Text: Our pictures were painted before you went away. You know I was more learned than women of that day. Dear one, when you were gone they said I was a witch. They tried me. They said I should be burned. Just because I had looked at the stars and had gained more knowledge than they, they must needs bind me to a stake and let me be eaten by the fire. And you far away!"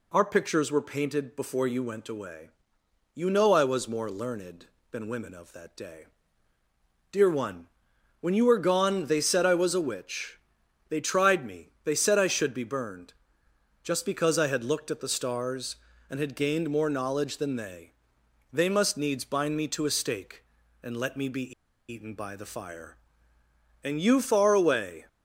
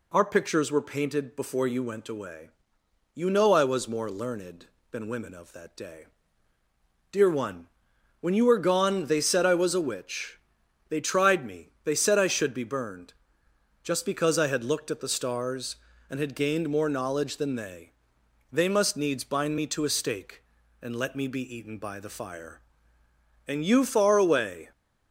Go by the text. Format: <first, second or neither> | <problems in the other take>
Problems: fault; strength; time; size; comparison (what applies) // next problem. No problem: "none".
second | pauses between "be" and "eaten"; at 21.5 s; 0.38 s long